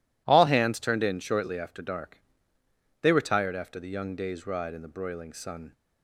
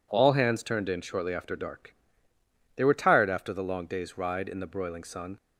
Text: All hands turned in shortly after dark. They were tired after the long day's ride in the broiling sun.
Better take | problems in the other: second | says "young" for "long"; at 3.8 s

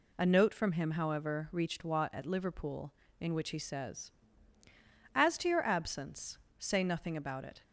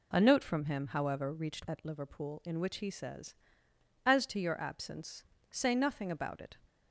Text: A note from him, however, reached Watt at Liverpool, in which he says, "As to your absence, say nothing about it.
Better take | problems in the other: first | skips "Watt"; at 1.6 s

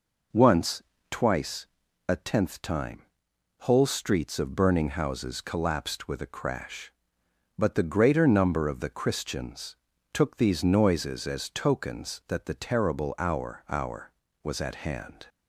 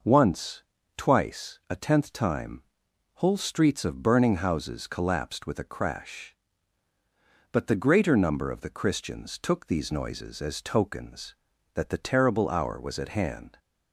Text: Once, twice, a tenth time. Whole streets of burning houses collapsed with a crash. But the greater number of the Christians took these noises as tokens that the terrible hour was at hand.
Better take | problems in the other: second | pauses between "Christians" and "took"; at 9.7 s; 0.38 s long // says "hour" twice; at 13.6 s

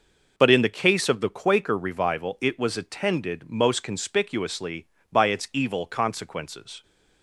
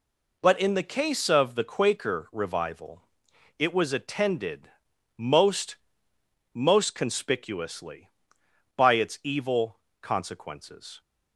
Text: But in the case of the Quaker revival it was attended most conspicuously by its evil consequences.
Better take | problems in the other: first | pauses between "revival" and "it"; noticeable; at 3.0 s; 0.56 s long // pauses between "attended" and "most"; noticeable; at 4.7 s; 0.46 s long // says "most" twice; at 6.5 s // pauses between "evil" and "consequences"; slight; at 9.7 s; 0.22 s long

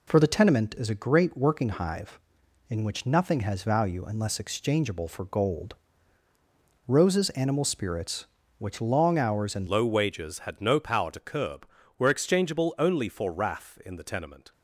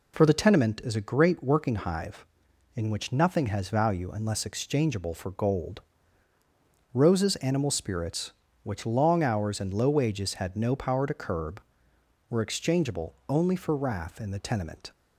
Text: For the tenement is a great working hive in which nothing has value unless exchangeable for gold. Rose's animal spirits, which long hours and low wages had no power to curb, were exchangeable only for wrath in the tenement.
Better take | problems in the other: second | changes voice at "low"; from 9.6 s on; 4.9 s long

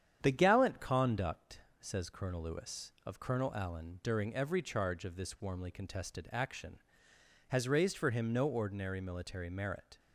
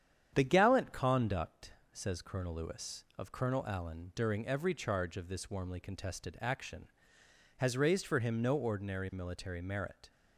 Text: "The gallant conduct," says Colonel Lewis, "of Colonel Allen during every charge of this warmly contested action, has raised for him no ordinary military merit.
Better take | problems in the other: neither | starts louder than the rest; strong; the same in both

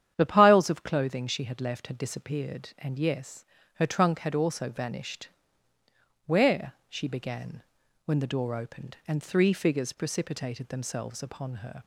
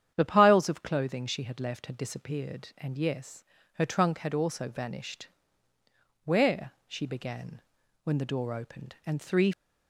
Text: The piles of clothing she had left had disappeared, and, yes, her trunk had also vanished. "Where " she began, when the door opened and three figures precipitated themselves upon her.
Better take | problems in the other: first | starts louder than the rest; strong; until 1.1 s; 9.5 dB; strong in the first // stops before "figures precipitated themselves upon her"; at 9.5 s

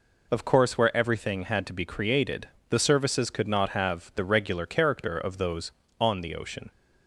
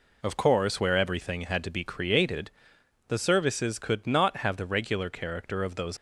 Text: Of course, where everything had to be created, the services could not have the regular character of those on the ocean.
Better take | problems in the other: first | stops before "on the ocean"; at 5.9 s

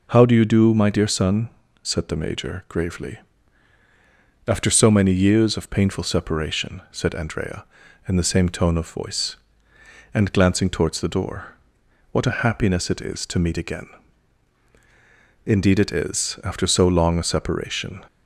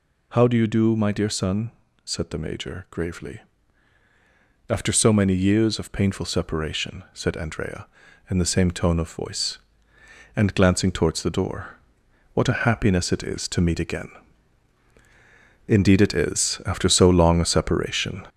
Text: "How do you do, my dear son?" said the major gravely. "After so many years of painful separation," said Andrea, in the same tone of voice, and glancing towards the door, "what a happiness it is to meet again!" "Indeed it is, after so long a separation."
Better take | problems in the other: first | gets louder; noticeable; throughout; 5 dB

